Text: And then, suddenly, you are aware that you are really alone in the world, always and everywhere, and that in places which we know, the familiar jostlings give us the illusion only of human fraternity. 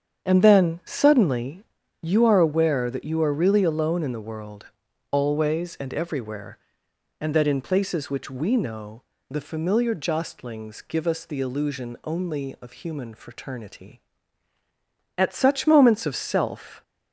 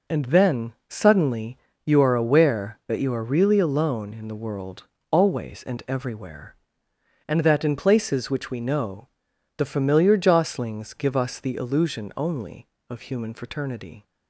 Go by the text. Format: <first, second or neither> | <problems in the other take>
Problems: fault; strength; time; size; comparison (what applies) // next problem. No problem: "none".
second | starts louder than the rest; strong; until 1.2 s; 8 dB // goes on to say "At such moments of self"; from 15.1 s on; 1.6 s long